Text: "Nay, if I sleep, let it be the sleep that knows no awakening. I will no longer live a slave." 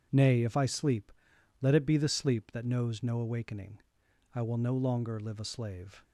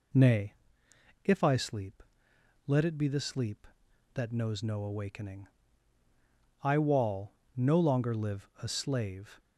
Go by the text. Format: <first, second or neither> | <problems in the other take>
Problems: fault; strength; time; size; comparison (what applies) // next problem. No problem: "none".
first | says "wall" for "will"; at 6.7 s